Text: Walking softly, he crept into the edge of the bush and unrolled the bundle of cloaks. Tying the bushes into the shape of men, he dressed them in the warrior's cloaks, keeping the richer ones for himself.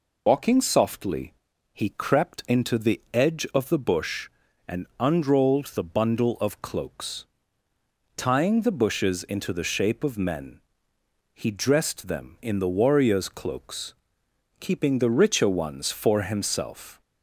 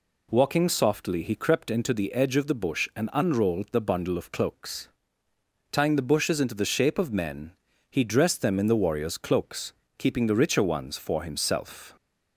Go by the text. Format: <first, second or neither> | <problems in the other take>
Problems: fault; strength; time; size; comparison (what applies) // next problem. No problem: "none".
second | loses the start of "Walking"; at 0.2 s; 90 ms